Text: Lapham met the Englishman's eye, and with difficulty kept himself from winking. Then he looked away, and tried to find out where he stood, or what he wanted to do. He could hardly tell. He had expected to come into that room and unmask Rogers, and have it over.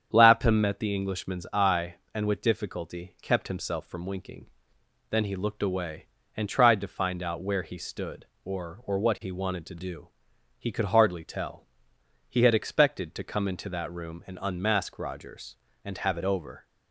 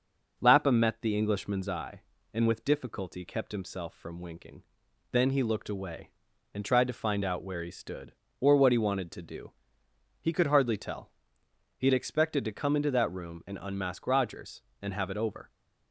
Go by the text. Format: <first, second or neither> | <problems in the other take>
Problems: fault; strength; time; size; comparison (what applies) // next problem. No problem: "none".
second | starts louder than the rest; strong; until 1.1 s; 8 dB // says "or" twice; at 8.8 s